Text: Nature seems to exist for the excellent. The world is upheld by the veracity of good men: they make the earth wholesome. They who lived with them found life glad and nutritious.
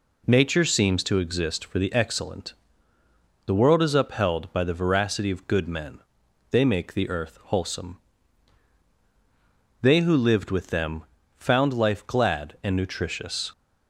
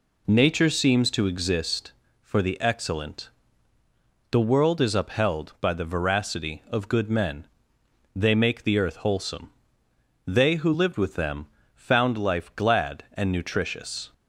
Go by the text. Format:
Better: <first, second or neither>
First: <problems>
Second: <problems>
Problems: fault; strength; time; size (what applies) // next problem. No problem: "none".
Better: neither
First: pauses between "them" and "found"; slight; at 11.0 s; 0.32 s long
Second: pauses between "them" and "found"; slight; at 11.4 s; 0.28 s long